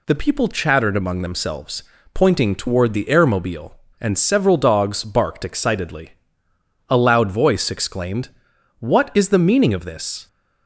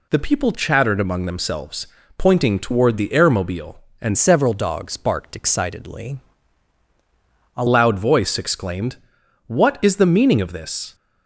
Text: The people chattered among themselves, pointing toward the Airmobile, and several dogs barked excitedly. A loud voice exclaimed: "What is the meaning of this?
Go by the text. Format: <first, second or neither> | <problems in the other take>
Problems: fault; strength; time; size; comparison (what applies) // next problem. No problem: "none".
first | changes voice from "several" to "A"; from 4.1 to 7.6 s; 3.5 s long